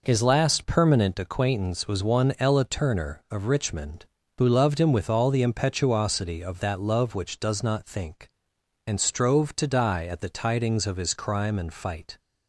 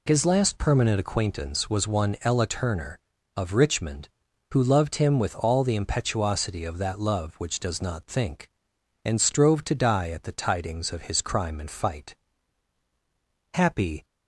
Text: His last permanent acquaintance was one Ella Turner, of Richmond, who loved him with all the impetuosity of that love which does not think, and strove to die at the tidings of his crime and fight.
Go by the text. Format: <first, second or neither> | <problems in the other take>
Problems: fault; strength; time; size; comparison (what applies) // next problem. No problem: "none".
first | goes on to say "Happy"; from 13.5 s on; 0.50 s long